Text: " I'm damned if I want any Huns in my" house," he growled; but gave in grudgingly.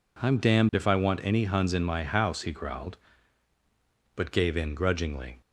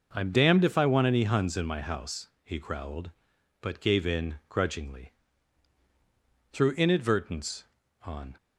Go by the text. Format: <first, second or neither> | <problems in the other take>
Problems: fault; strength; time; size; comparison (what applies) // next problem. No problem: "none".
first | goes on to say "Through inadvertence on"; strong; from 6.5 s on; 1.8 s long